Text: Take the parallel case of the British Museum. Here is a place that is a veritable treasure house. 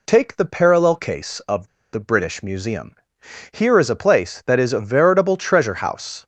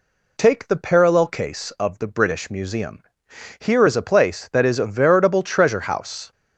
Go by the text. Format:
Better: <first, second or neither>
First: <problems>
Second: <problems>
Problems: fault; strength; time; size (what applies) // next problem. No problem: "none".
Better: second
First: pauses between "of" and "the"; slight; at 1.6 s; 0.25 s long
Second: none